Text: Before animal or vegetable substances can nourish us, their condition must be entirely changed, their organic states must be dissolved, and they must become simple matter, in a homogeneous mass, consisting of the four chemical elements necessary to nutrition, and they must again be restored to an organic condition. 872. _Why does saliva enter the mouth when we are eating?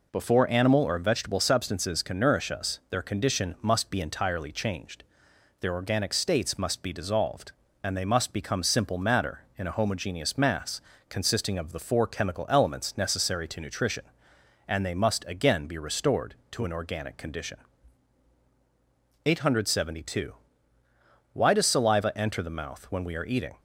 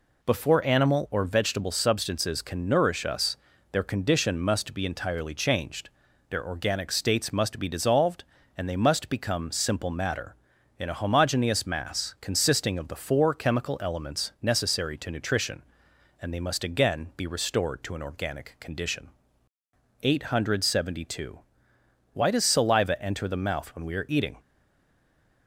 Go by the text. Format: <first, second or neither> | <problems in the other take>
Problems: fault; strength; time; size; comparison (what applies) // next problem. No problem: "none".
first | stays silent after the last word; from 24.3 s on; 1.1 s long